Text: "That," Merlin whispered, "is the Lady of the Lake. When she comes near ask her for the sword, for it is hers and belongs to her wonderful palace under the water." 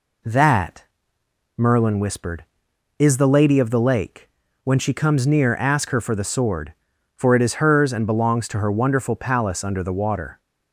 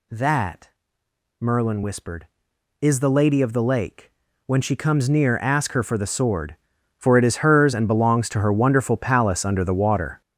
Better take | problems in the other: first | gets louder; strong; throughout; 10 dB

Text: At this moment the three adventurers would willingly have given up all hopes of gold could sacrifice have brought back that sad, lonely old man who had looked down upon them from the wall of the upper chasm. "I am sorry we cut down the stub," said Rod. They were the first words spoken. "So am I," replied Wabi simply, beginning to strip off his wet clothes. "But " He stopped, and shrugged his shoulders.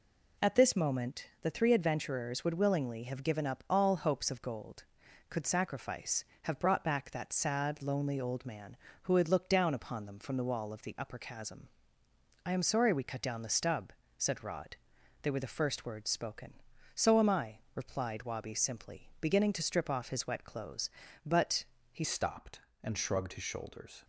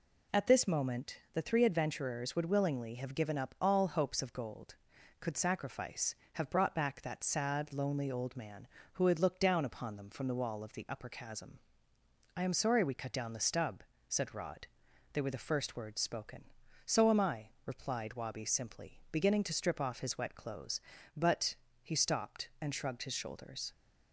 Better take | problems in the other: second | pauses between "moment" and "the"; slight; at 1.2 s; 0.16 s long; slight in the second // changes voice at "stopped"; from 22.0 s on; 2.0 s long

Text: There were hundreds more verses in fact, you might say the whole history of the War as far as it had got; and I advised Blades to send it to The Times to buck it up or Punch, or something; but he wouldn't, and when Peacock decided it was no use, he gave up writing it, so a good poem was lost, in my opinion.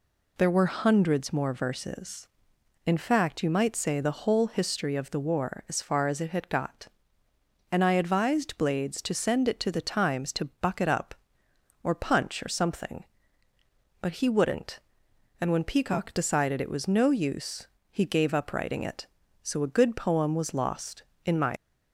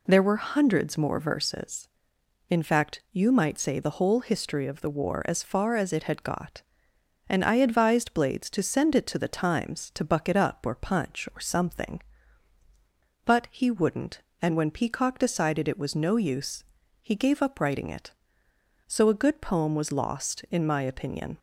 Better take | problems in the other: second | stops before "opinion"; at 21.5 s

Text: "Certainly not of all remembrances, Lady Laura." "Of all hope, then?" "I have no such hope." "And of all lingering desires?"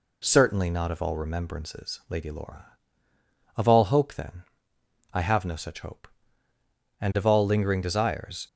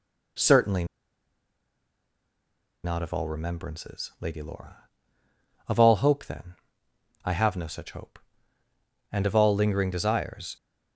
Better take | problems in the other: first | pauses between "Certainly" and "not"; strong; at 0.8 s; 1.9 s long

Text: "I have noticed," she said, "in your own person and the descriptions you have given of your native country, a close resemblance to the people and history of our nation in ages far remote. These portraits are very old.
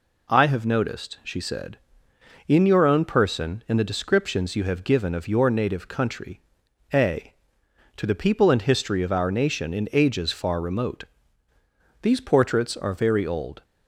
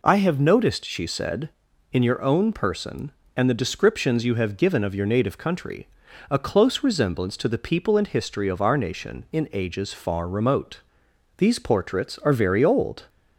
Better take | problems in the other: second | skips "close resemblance"; at 7.6 s

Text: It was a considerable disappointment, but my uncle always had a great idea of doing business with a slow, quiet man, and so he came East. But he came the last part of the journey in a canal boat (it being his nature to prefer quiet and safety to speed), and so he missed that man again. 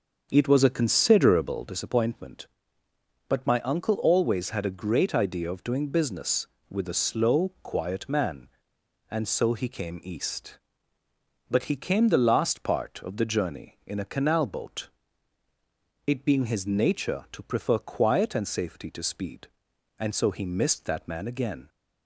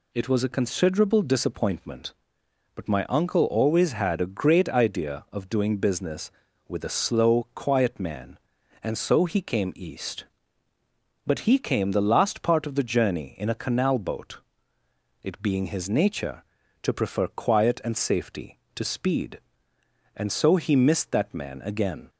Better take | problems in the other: second | starts louder than the rest; until 1.9 s; 6.5 dB

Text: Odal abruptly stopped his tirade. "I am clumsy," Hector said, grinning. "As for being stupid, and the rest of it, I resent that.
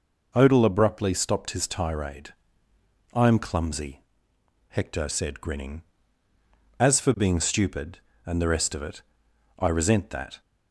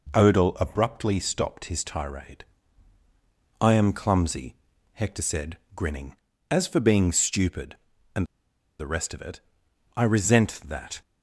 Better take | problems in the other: first | pauses between "and" and "the"; noticeable; at 8.2 s; 0.53 s long

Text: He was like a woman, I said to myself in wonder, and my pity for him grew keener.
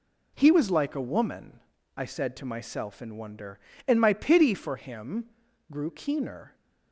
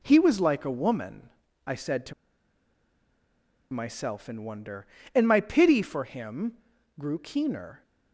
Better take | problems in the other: first | pauses between "to" and "myself"; strong; at 2.1 s; 1.5 s long // pauses between "him" and "grew"; at 6.5 s; 0.44 s long; also in the first

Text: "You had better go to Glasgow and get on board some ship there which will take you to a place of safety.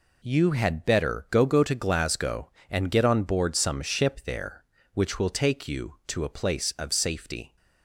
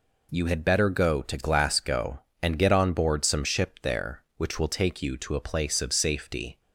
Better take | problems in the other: second | says "go" twice; at 1.4 s

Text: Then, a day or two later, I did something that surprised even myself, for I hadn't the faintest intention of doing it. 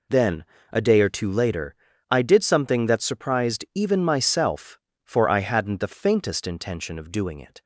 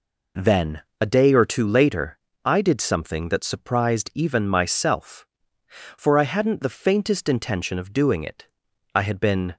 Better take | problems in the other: first | goes on to say "I had been"; noticeable; from 8.9 s on; 0.62 s long

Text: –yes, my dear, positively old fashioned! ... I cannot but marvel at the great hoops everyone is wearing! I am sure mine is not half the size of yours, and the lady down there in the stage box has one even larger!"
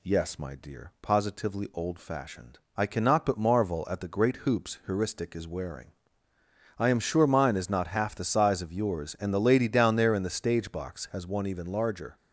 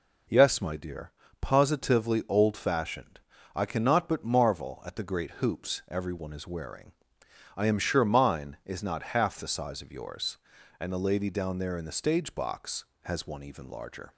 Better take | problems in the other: second | says "heuristic" for "everyone"; at 4.8 s

